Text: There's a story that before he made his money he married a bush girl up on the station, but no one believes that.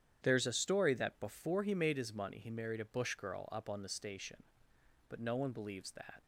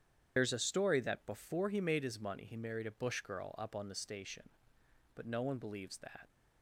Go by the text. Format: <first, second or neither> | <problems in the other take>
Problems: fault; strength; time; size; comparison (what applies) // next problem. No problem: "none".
first | loses the start of "There's"; at 0.3 s; 65 ms // starts louder than the rest; strong; until 1.3 s; 9 dB; strong in the first